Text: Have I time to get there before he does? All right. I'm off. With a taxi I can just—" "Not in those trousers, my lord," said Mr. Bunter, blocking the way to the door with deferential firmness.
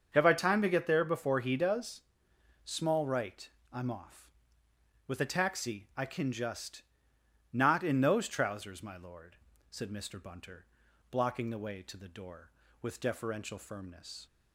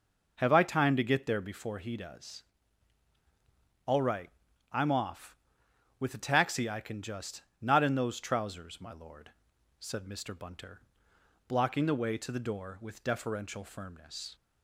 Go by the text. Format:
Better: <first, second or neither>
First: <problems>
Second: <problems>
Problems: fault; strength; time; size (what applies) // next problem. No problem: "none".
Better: second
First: starts louder than the rest; until 1.1 s; 6.5 dB // says "Small" for "All"; at 2.6 s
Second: none